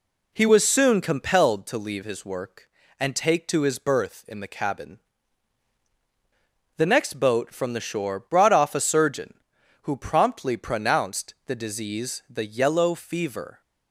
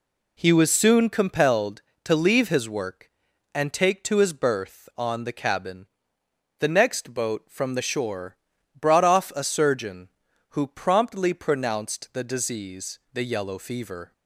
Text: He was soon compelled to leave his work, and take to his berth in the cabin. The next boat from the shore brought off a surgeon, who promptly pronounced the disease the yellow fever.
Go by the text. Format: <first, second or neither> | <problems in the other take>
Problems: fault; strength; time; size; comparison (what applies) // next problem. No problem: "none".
first | says "on" for "in"; at 4.9 s // pauses between "shore" and "brought"; at 8.3 s; 0.42 s long // pauses between "disease" and "the"; slight; at 12.9 s; 0.16 s long